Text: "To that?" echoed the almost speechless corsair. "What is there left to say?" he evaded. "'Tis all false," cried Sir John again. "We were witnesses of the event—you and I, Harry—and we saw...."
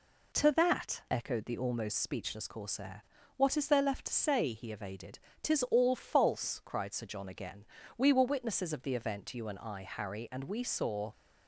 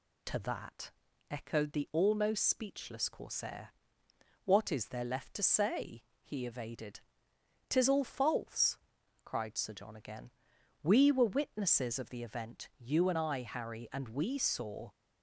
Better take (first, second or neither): neither